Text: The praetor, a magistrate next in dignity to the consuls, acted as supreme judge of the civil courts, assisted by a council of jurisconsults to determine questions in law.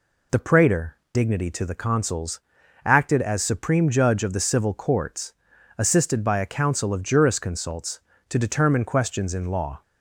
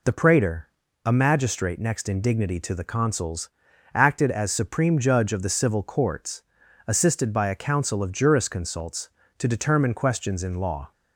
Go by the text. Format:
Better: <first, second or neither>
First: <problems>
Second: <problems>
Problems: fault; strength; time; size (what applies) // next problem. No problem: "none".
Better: second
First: skips "a magistrate next in"; at 1.0 s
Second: none